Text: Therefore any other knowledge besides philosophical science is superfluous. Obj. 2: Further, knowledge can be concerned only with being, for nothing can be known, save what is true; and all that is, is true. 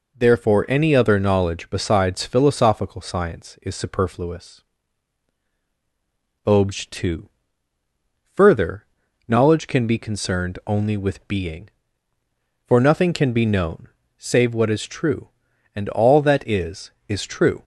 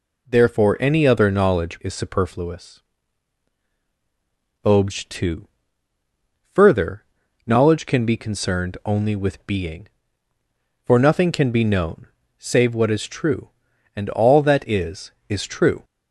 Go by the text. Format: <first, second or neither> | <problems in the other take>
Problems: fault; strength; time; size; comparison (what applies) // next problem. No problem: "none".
first | skips "besides philosophical science"; at 1.8 s